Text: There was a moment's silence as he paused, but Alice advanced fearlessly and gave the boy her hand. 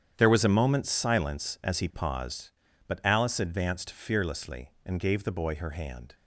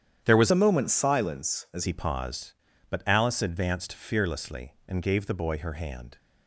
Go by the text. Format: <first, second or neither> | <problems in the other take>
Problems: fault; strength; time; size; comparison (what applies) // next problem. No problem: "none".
first | starts louder than the rest; strong; until 1.2 s; 10 dB; strong in the first // changes voice from "a" to "as"; from 0.5 to 1.8 s; 1.3 s long